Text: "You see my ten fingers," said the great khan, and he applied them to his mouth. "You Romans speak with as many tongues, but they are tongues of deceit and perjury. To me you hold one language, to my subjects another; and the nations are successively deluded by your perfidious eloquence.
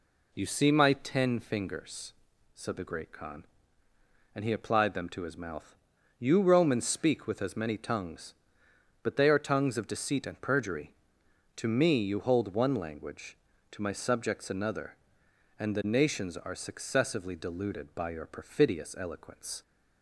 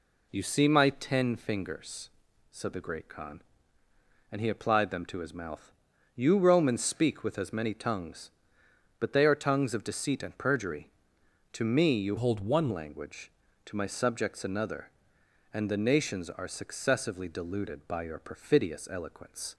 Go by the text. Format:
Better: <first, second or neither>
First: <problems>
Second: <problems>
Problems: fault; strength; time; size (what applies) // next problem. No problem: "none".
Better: first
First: none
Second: changes voice from "hold" to "one"; from 12.1 to 12.7 s; 0.6 s long